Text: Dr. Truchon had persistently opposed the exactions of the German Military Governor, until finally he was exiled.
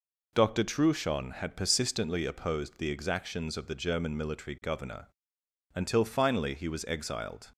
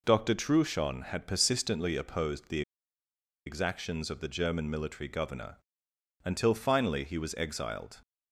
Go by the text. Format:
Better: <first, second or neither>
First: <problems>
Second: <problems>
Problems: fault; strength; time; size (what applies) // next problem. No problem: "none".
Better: first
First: none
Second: pauses between "the" and "exactions"; noticeable; at 2.6 s; 0.85 s long